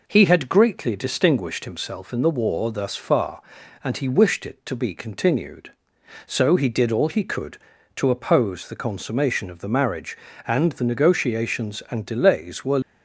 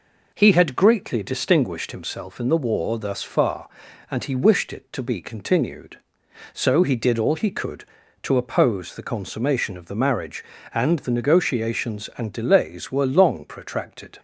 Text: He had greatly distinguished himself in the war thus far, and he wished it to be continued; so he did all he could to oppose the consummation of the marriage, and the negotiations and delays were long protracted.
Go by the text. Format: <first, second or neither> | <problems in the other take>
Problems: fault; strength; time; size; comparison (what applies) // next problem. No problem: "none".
second | stops before "long protracted"; at 12.8 s